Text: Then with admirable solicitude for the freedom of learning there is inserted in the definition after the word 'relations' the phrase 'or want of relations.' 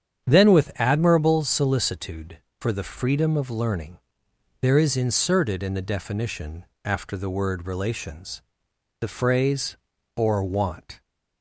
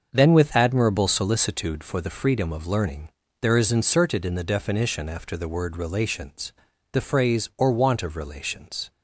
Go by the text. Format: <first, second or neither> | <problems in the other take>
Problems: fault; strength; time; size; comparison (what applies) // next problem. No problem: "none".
second | starts louder than the rest; strong; until 1.3 s; 8 dB; also in the second // pauses between "learning" and "there"; noticeable; at 3.9 s; 0.62 s long; slight in the second // pauses between "definition" and "after"; slight; at 6.6 s; 0.22 s long // pauses between "relations" and "the"; noticeable; at 8.4 s; 0.60 s long; also in the second // stops before "of relations"; at 11.0 s